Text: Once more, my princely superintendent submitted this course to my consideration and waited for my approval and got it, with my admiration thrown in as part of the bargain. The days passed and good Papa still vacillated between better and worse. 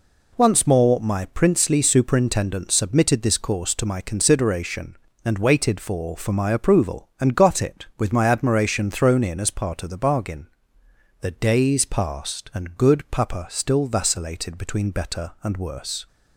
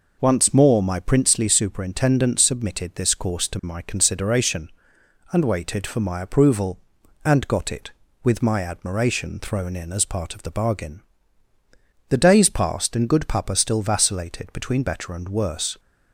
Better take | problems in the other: second | says "for" twice; at 6.1 s

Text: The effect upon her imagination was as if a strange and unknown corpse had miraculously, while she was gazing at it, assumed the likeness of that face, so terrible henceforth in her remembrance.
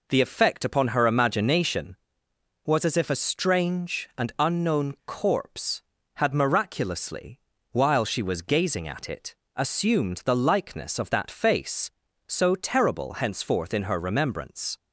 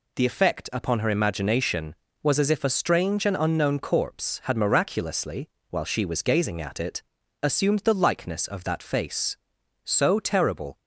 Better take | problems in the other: first | stops before "henceforth in her remembrance"; at 10.7 s

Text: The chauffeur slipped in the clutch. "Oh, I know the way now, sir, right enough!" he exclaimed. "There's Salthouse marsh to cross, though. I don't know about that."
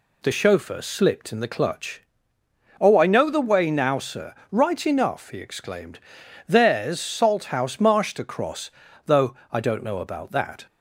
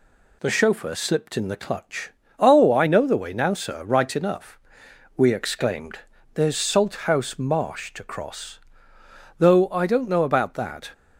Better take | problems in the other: first | says "we" for "he"; at 5.1 s

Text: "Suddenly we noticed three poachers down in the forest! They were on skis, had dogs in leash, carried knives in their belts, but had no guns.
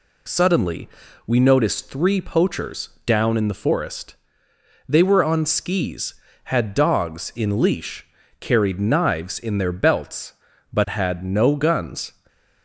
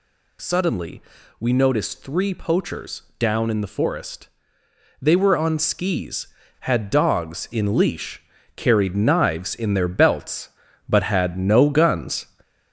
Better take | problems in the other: first | gets louder; noticeable; throughout; 6 dB // pauses between "Suddenly" and "we"; slight; at 1.0 s; 0.36 s long; slight in the first // pauses between "poachers" and "down"; slight; at 3.0 s; 0.16 s long; slight in the first

